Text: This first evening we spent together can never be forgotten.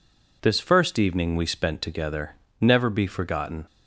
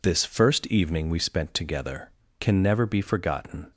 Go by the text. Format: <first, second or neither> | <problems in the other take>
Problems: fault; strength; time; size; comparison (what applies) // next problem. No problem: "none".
second | skips "can"; at 2.4 s